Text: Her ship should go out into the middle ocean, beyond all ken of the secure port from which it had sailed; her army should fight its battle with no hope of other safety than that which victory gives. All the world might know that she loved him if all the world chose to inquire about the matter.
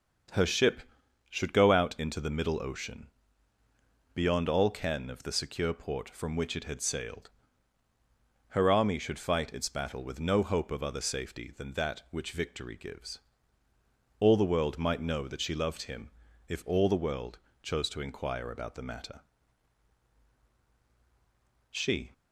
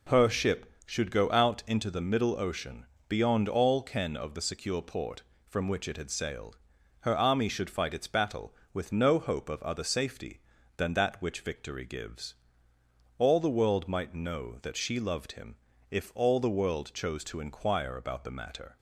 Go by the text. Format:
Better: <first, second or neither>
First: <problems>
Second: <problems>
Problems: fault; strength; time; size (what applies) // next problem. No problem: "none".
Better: second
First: starts louder than the rest; until 1.7 s; 6.5 dB // pauses between "him" and "if"; slight; at 16.1 s; 0.36 s long // pauses between "world" and "chose"; slight; at 17.3 s; 0.24 s long // goes on to say "She"; slight; from 21.7 s on; 0.42 s long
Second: pauses between "him" and "if"; slight; at 15.5 s; 0.34 s long